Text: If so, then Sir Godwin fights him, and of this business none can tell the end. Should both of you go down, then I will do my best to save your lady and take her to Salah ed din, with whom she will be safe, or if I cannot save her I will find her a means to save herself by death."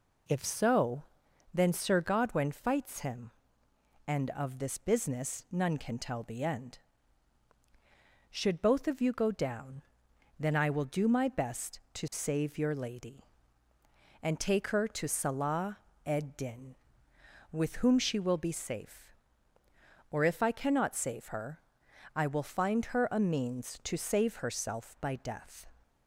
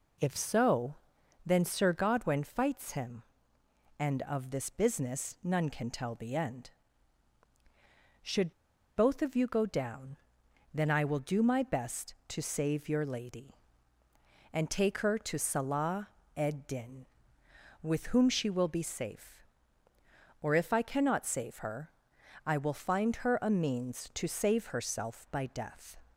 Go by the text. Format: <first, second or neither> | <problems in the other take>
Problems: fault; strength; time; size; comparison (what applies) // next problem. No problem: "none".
first | pauses between "Should" and "both"; at 8.5 s; 0.44 s long // pauses between "Salah" and "ed"; slight; at 16.0 s; 0.28 s long; slight in the first // pauses between "her" and "I"; noticeable; at 21.9 s; 0.54 s long; noticeable in the first